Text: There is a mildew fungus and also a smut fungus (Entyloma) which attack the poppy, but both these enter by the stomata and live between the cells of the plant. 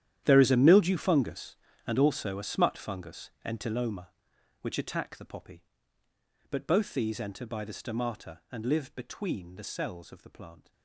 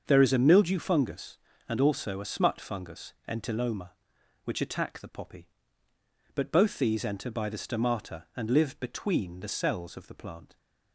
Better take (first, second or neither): second